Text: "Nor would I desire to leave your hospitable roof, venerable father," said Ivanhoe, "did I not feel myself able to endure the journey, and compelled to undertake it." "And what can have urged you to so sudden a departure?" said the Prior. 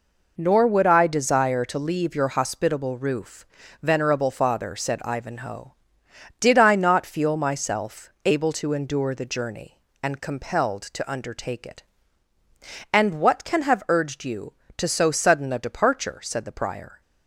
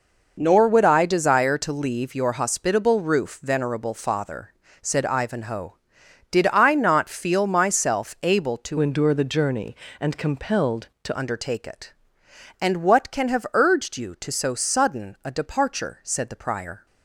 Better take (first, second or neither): first